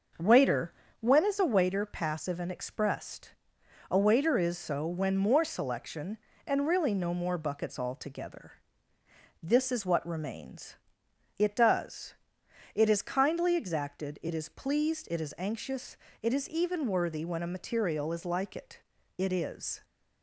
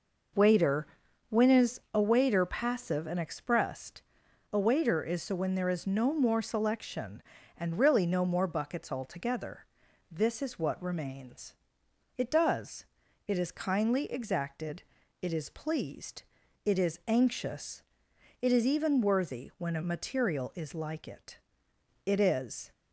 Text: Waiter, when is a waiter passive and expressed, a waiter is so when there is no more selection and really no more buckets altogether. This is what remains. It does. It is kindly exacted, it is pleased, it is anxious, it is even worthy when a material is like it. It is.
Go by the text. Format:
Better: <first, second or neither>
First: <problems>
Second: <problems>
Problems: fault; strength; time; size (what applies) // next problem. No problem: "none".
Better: second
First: starts louder than the rest; until 1.4 s; 6 dB // skips "there is no"; at 5.1 s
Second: none